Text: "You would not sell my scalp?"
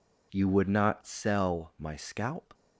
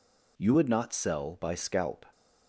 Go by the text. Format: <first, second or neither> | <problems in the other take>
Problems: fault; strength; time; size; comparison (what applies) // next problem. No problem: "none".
first | says "by" for "my"; at 1.3 s